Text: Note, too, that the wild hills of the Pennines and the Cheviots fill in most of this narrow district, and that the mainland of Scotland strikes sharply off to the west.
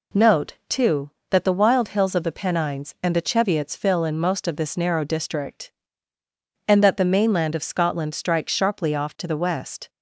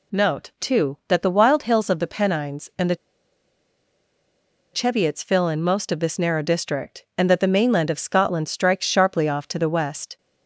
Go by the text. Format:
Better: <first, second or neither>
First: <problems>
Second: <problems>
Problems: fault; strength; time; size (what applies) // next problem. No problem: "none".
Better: first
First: none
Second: pauses between "the" and "Cheviots"; strong; at 2.9 s; 1.7 s long